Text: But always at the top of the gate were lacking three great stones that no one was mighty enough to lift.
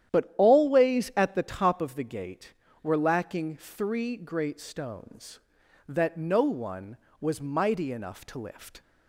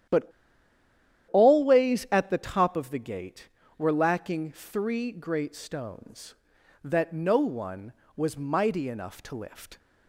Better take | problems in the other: first | starts louder than the rest; strong; until 2.1 s; 10.5 dB; strong in the first // pauses between "But" and "always"; at 0.3 s; 1.0 s long

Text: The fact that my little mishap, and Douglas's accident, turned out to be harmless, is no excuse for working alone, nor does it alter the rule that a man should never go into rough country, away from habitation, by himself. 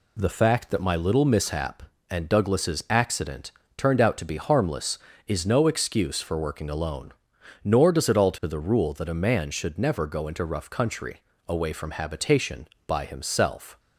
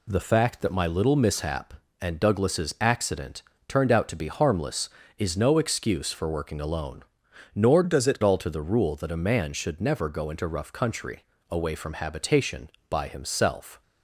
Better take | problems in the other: first | changes voice from "does" to "it"; from 7.8 to 8.1 s; 0.3 s long

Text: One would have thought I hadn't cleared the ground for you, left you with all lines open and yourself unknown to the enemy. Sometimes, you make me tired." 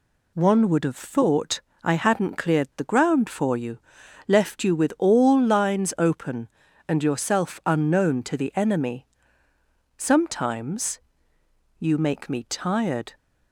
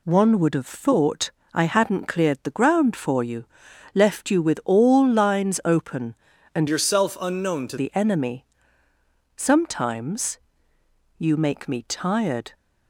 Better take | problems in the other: first | pauses between "thought" and "I"; slight; at 1.3 s; 0.22 s long; slight in the first // changes voice from "yourself" to "to"; from 6.6 to 7.7 s; 1.1 s long

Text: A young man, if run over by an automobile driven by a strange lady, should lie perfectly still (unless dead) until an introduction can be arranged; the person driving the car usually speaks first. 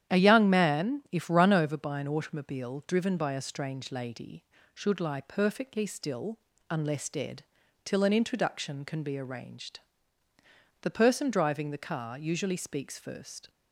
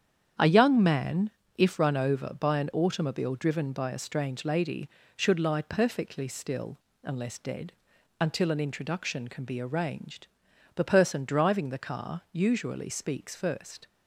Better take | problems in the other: second | starts louder than the rest; strong; until 1.1 s; 10 dB; strong in the second // says "till" for "until"; at 7.8 s

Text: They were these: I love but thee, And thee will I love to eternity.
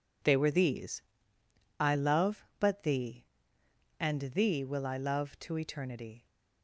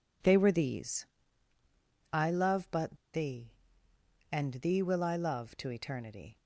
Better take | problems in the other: first | pauses between "but" and "thee"; slight; at 2.9 s; 0.17 s long

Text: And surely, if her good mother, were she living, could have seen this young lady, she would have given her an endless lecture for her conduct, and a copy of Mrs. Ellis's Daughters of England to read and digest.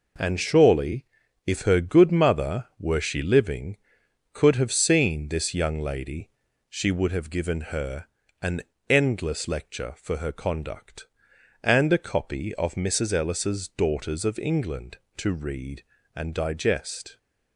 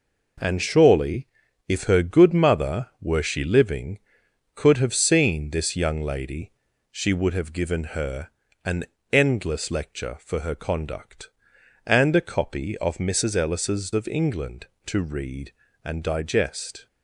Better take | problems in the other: first | pauses between "her" and "an"; slight; at 8.2 s; 0.36 s long; slight in the first // pauses between "an" and "endless"; slight; at 8.8 s; 0.28 s long; slight in the first // skips "Daughters"; at 13.9 s

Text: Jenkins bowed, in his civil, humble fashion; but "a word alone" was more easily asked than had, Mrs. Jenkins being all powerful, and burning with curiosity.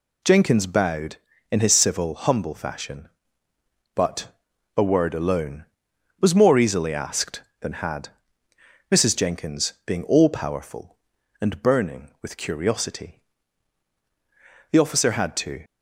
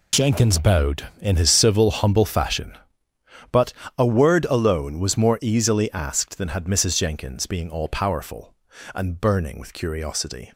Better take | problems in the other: second | pauses between "but" and "a"; noticeable; at 4.2 s; 0.48 s long; slight in the second // goes on to say "The officer had to"; noticeable; from 14.7 s on; 0.94 s long

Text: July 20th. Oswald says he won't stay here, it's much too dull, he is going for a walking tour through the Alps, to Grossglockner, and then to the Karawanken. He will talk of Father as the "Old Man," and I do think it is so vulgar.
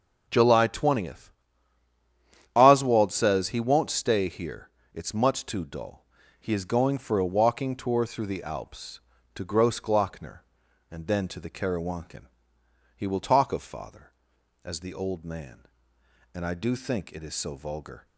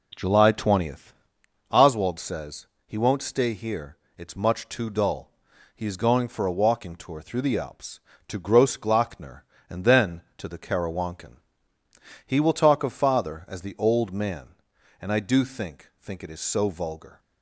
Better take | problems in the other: first | pauses between "says" and "he"; slight; at 2.6 s; 0.18 s long // says "think" twice; at 15.9 s

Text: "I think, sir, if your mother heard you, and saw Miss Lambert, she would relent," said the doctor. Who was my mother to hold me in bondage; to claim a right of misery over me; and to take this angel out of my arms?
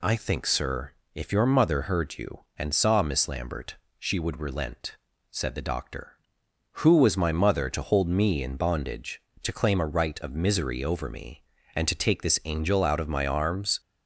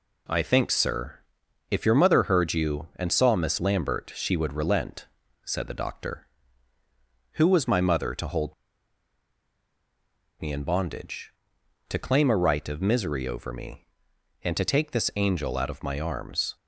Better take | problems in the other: first | pauses between "hold" and "me"; strong; at 8.5 s; 1.8 s long

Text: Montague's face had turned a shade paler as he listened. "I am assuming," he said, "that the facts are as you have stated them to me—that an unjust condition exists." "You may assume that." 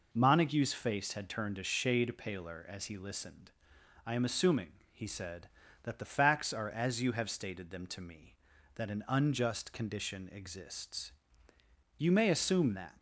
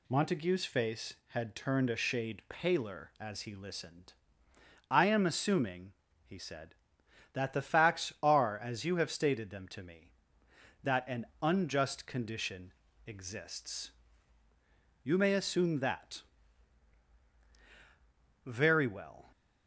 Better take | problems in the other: first | pauses between "an" and "unjust"; slight; at 11.2 s; 0.16 s long // pauses between "condition" and "exists"; slight; at 12.7 s; 0.36 s long // goes on to say "Very well"; noticeable; from 18.4 s on; 0.86 s long

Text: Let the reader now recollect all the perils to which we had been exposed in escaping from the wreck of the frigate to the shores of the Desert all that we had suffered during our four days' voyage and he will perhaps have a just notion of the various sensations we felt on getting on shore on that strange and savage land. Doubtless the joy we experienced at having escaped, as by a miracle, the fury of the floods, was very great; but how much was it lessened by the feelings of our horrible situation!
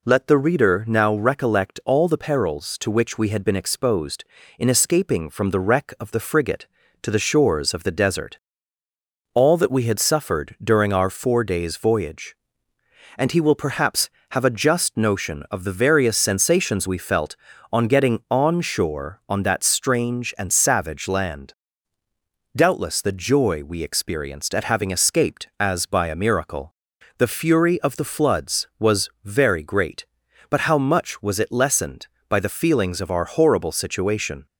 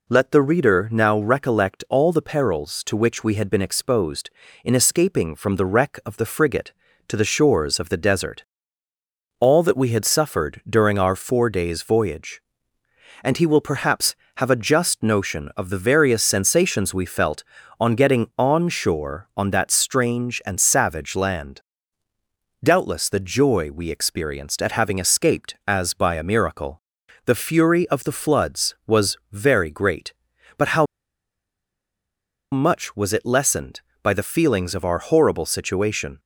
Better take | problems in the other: first | pauses between "Desert" and "all"; noticeable; at 8.4 s; 0.96 s long; noticeable in the first // pauses between "how" and "much"; strong; at 30.8 s; 1.6 s long

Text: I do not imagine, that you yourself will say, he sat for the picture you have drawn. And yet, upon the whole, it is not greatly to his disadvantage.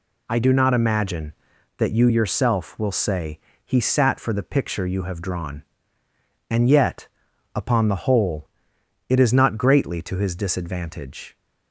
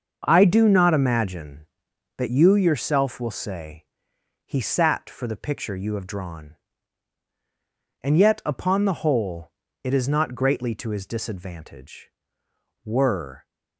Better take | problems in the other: first | starts louder than the rest; until 1.2 s; 6.5 dB // goes on to say "Were"; from 12.8 s on; 0.60 s long

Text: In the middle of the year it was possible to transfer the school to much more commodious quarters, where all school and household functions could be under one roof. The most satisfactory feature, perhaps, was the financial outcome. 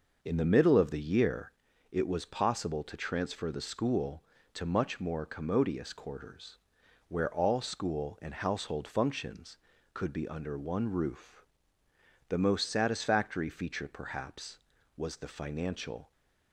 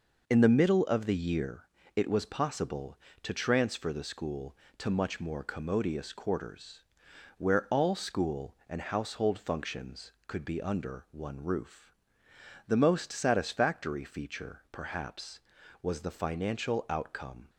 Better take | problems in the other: second | pauses between "year" and "it"; at 1.5 s; 0.38 s long; slight in the second // stops before "outcome"; at 16.1 s

